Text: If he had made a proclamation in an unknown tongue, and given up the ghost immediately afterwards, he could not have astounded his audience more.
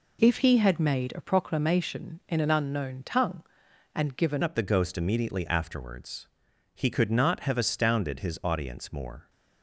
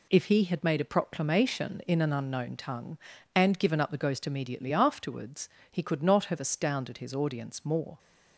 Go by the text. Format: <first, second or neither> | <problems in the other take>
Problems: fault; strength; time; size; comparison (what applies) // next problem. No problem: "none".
second | changes voice at "up"; from 4.4 s on; 4.8 s long